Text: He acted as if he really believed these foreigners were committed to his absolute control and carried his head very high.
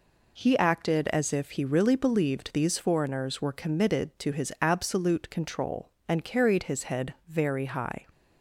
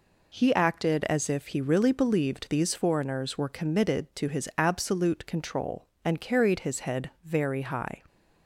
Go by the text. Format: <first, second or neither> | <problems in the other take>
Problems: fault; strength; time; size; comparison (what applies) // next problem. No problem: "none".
neither | none